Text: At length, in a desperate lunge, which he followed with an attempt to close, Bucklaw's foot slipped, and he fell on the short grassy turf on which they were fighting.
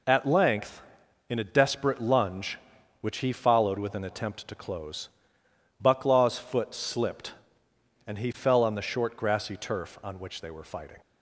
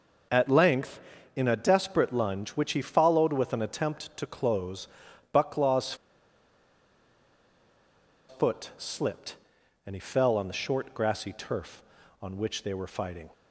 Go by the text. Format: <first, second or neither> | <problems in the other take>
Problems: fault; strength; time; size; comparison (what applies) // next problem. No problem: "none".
first | pauses between "Bucklaw's" and "foot"; strong; at 5.9 s; 2.3 s long